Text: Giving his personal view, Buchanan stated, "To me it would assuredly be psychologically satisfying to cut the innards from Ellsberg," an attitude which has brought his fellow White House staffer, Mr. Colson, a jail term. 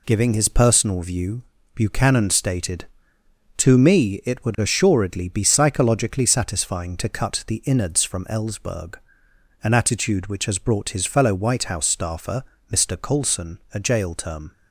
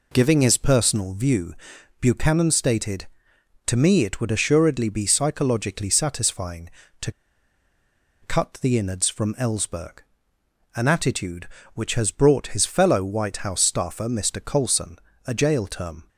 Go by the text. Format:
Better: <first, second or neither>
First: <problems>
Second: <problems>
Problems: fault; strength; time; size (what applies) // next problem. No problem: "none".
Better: first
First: none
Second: pauses between "to" and "cut"; at 7.1 s; 1.1 s long